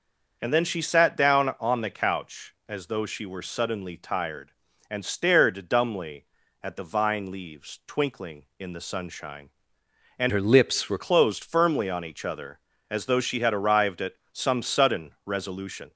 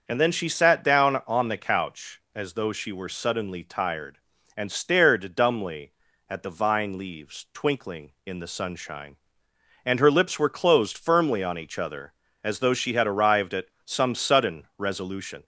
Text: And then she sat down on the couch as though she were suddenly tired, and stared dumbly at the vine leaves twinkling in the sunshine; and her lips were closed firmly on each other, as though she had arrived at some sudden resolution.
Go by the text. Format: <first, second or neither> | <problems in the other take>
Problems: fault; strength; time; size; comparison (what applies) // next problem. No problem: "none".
second | starts louder than the rest; until 1.4 s; 6.5 dB; also in the second // changes voice from "her" to "were"; from 10.2 to 10.9 s; 0.7 s long // pauses between "at" and "some"; slight; at 14.1 s; 0.18 s long; slight in the second